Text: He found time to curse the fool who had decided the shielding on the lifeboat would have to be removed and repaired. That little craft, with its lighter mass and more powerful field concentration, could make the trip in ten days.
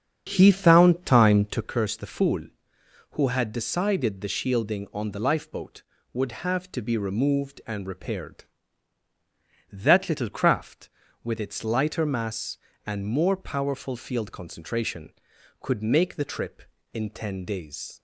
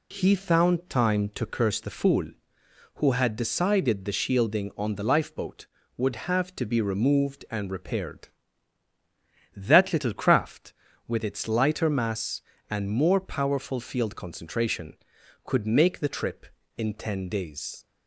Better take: second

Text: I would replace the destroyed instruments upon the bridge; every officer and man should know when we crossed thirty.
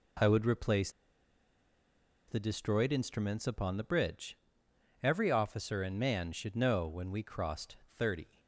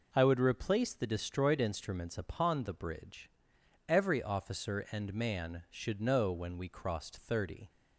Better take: second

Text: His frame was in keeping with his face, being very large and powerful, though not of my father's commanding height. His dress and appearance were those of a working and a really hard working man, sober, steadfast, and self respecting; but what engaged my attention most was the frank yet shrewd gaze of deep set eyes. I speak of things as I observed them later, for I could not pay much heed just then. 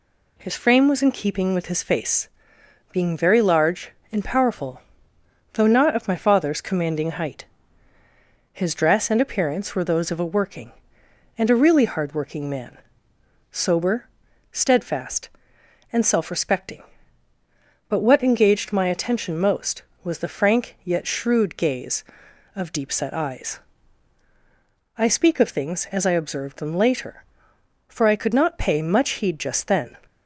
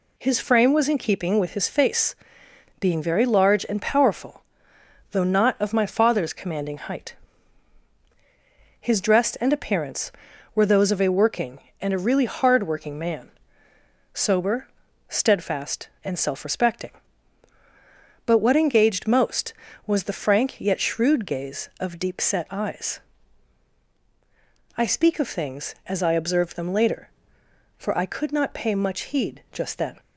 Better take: first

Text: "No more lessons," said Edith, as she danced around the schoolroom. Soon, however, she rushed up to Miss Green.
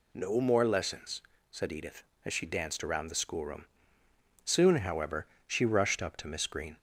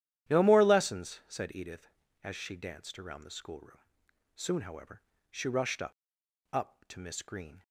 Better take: first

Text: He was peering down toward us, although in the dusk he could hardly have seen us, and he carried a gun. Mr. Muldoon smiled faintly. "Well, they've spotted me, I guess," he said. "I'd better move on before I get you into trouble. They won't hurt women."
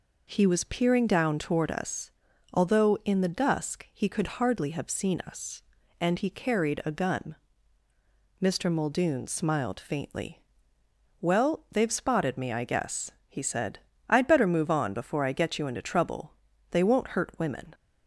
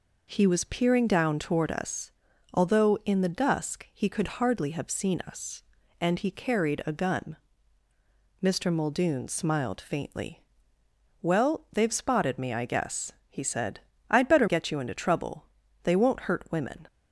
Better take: first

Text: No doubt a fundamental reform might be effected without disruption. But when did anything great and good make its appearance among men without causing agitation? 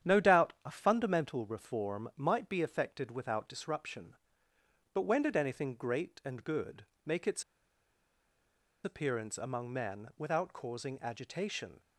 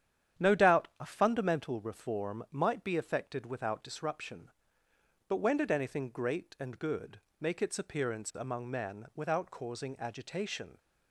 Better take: second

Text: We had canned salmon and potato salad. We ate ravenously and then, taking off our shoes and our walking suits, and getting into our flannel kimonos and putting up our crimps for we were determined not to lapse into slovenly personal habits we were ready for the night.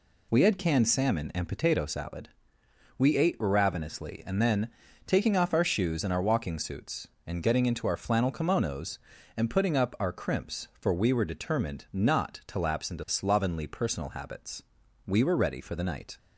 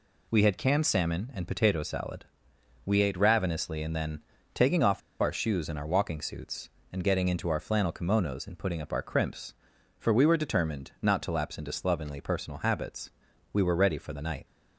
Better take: first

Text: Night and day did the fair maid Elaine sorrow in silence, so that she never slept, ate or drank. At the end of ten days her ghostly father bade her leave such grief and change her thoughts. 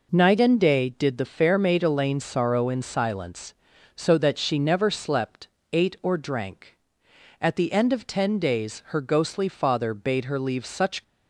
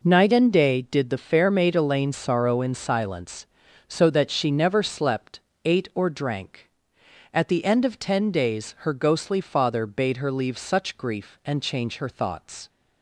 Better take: second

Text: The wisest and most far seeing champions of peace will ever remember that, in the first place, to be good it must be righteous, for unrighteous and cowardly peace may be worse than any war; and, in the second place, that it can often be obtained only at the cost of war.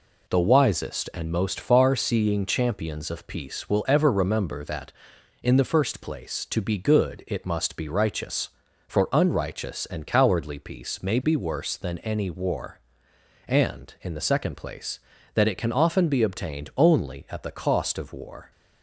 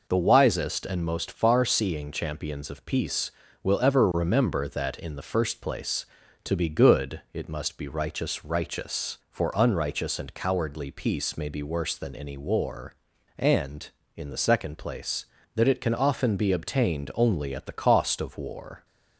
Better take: first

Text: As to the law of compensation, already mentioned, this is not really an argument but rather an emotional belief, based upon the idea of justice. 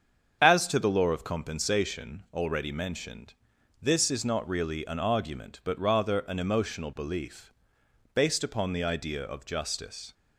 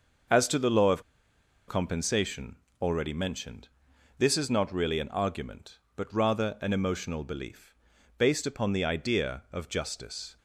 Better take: first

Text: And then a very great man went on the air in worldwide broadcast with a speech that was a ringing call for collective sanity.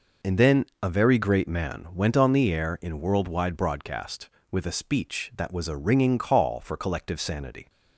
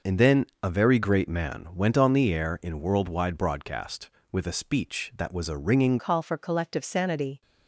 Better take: first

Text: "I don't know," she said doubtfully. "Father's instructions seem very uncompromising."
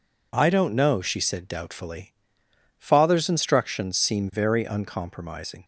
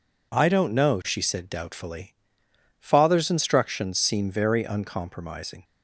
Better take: neither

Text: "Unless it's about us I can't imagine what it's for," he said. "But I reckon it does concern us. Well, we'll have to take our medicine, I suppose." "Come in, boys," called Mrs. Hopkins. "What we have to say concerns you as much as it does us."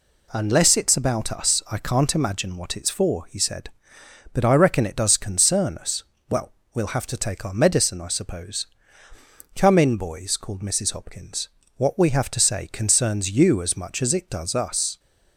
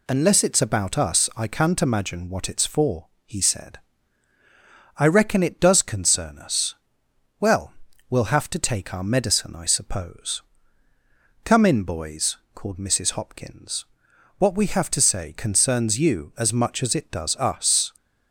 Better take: first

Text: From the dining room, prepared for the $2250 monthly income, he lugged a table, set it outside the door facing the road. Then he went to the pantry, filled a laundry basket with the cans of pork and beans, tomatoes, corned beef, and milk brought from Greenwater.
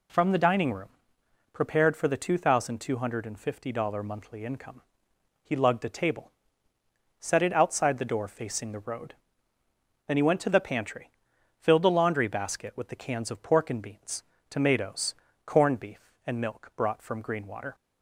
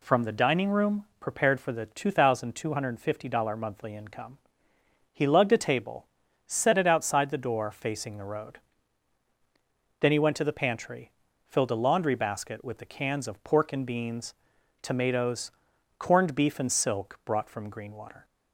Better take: first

